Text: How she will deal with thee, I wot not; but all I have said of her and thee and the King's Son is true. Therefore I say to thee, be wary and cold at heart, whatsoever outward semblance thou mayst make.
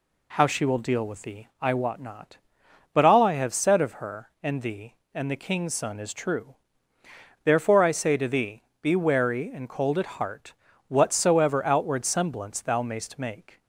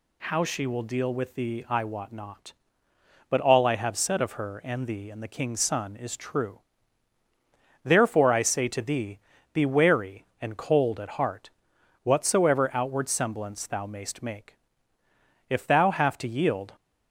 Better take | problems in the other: first | goes on to say "If thou have to yield"; noticeable; from 15.4 s on; 1.2 s long

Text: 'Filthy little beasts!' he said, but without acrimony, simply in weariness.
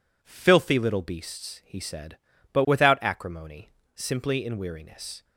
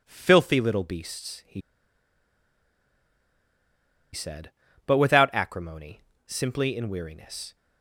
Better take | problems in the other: first | pauses between "he" and "said"; strong; at 1.6 s; 2.5 s long

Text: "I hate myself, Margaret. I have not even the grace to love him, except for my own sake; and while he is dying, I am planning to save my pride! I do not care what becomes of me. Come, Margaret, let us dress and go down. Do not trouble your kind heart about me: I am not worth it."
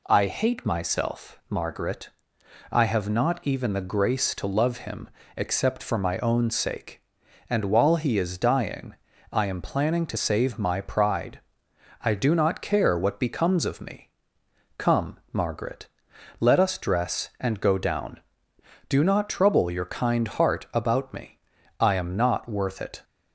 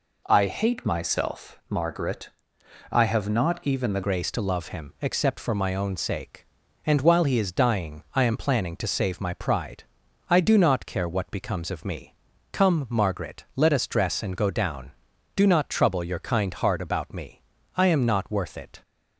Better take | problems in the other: first | changes voice at "grace"; from 4.0 s on; 14.8 s long

